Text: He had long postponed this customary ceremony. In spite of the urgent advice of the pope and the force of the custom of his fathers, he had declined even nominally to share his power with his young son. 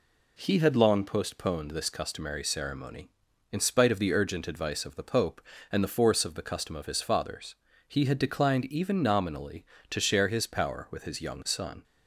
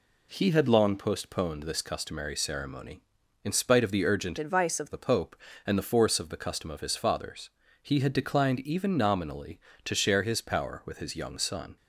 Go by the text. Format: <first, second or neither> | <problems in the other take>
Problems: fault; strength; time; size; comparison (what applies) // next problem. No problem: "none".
first | changes voice from "advice" to "of"; from 4.3 to 4.9 s; 0.6 s long